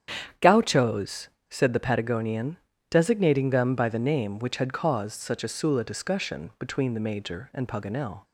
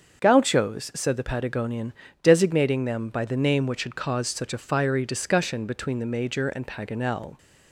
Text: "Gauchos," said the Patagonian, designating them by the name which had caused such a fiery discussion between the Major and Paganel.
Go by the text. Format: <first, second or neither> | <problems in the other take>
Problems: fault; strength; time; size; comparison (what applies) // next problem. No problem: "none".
second | starts louder than the rest; strong; until 1.6 s; 9 dB; also in the second // says "sula" for "fiery"; at 5.4 s